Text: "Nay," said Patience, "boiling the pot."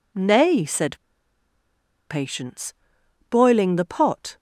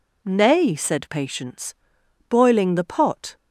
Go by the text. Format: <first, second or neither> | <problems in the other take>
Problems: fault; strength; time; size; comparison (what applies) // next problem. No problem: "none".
second | pauses between "said" and "Patience"; at 0.9 s; 1.1 s long